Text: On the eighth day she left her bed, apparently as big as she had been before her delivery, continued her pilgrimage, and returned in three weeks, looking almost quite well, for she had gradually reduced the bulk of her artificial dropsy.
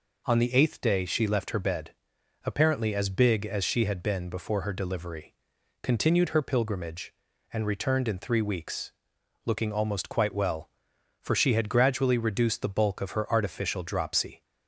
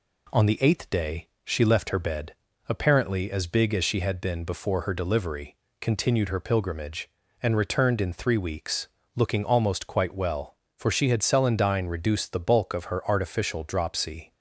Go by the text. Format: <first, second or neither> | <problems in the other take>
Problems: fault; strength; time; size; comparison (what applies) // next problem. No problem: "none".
first | pauses between "day" and "she"; slight; at 1.2 s; 0.18 s long // says "celandine" for "gradually"; at 11.2 s